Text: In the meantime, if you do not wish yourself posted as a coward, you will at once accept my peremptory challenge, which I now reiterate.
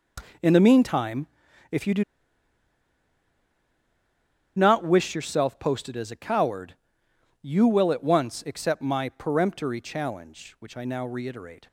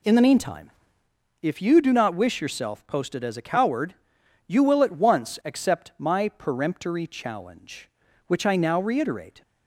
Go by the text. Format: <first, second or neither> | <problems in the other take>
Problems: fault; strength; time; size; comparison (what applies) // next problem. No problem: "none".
second | pauses between "do" and "not"; strong; at 2.0 s; 2.5 s long